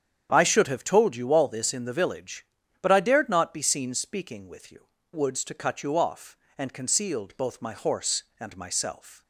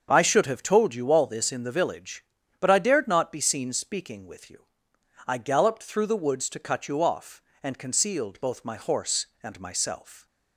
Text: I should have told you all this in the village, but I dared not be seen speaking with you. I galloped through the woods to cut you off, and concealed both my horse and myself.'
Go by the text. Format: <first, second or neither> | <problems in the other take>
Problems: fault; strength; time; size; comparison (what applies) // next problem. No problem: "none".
second | starts louder than the rest; strong; until 1.3 s; 8.5 dB; also in the second // skips "I galloped through the"; at 4.9 s